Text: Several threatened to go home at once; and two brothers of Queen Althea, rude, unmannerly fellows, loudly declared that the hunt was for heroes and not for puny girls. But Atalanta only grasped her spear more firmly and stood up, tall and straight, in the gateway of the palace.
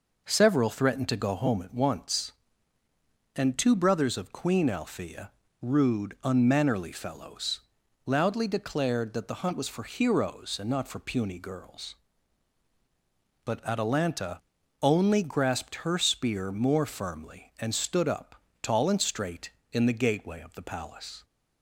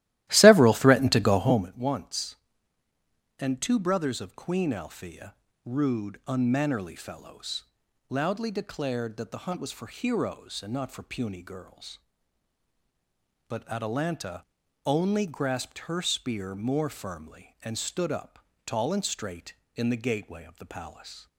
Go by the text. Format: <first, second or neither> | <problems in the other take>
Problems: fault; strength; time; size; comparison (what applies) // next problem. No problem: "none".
first | starts louder than the rest; strong; until 1.8 s; 15 dB // pauses between "Atalanta" and "only"; at 14.4 s; 0.42 s long; also in the first